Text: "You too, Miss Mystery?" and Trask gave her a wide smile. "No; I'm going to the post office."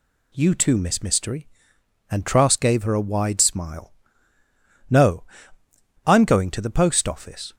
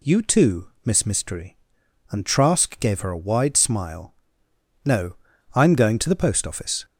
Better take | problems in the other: neither | none

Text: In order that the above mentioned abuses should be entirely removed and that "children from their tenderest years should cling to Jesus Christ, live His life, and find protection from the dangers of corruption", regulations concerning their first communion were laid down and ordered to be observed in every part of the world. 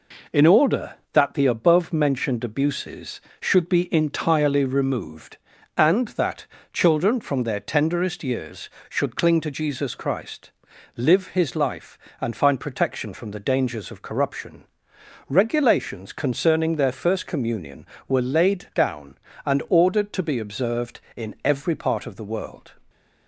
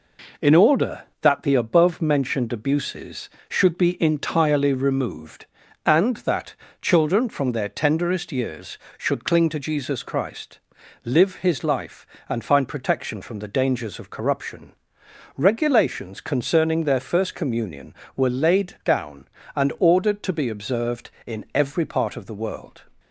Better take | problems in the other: neither | pauses between "that" and "children"; slight; the same in both

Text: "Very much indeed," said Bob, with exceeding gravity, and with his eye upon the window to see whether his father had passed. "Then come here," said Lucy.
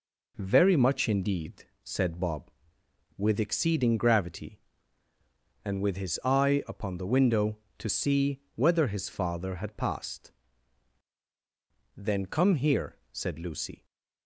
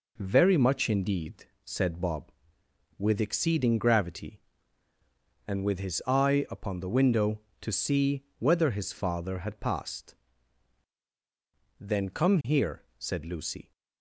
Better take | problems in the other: neither | none

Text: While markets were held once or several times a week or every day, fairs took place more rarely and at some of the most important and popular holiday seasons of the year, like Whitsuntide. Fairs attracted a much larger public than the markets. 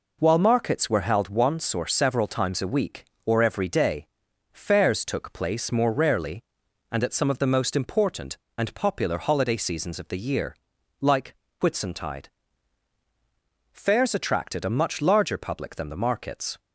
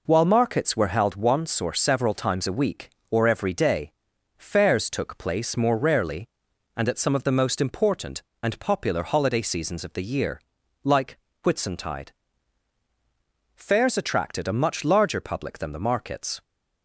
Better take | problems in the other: neither | pauses between "like" and "Whitsuntide"; slight; the same in both

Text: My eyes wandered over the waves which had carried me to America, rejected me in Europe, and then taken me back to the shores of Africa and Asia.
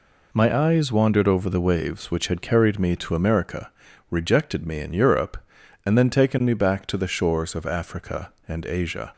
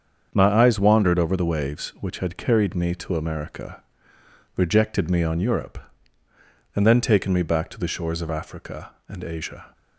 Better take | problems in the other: first | starts louder than the rest; strong; until 1.3 s; 7 dB // says "on" for "in"; at 5.2 s

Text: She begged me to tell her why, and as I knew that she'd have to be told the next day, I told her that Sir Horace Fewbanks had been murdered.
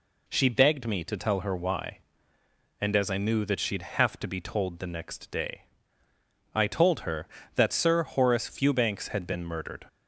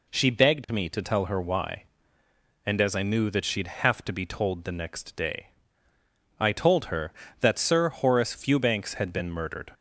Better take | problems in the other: neither | none

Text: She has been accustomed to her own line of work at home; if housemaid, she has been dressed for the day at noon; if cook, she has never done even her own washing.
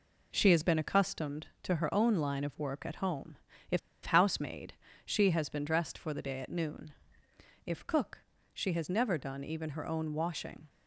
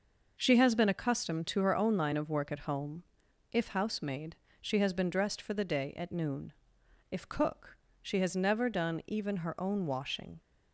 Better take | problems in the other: second | pauses between "if" and "housemaid"; slight; at 3.7 s; 0.27 s long

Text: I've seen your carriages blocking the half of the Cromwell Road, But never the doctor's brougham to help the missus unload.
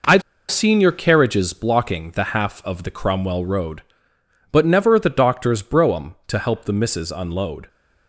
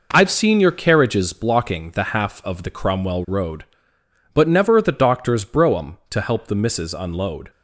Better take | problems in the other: second | pauses between "I've" and "seen"; slight; at 0.2 s; 0.29 s long

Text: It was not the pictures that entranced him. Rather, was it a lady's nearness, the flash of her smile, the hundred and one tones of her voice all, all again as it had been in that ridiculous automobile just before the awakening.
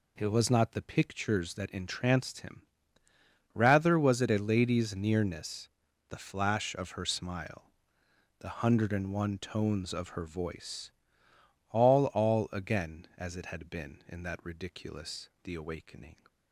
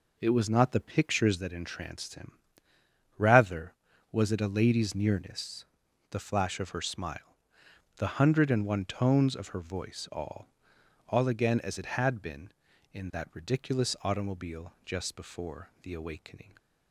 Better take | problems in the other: second | pauses between "voice" and "all"; noticeable; at 10.9 s; 0.78 s long // skips "automobile just before"; at 15.3 s

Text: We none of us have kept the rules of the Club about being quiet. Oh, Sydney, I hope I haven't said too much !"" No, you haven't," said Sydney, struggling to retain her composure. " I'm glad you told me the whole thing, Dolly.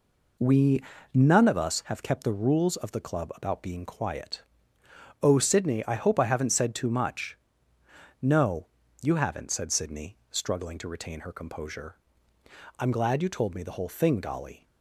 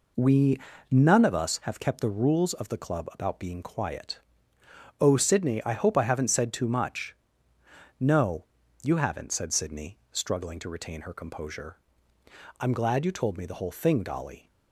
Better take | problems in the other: neither | pauses between "We" and "none"; slight; the same in both

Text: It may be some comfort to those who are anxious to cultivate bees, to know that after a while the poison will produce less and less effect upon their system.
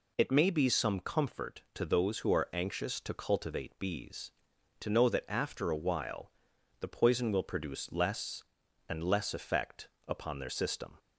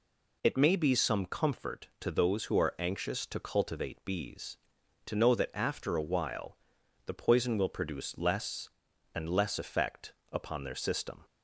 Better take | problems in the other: neither | pauses between "while" and "the"; noticeable; the same in both // pauses between "effect" and "upon"; slight; the same in both

